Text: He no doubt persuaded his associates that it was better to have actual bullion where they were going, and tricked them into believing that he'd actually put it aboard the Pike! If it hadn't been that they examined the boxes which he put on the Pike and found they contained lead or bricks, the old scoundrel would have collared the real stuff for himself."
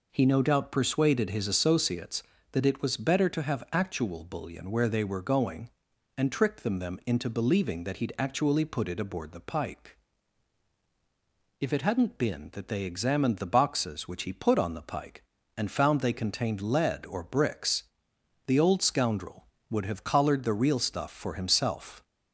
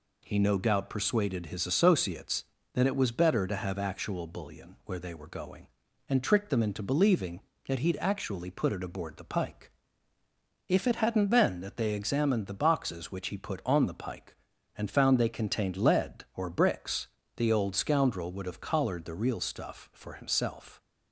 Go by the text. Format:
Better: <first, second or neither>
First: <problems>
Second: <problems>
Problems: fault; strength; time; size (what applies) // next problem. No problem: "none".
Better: second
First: says "them" twice; at 6.7 s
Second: none